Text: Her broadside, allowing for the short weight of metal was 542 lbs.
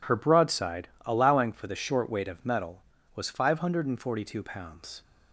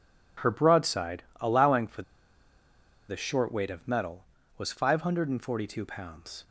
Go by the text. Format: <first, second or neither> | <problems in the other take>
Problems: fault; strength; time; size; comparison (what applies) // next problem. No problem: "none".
first | pauses between "for" and "the"; at 2.0 s; 1.0 s long